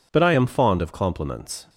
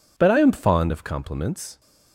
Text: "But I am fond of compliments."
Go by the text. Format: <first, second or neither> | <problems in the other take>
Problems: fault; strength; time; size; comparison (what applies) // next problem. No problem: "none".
neither | none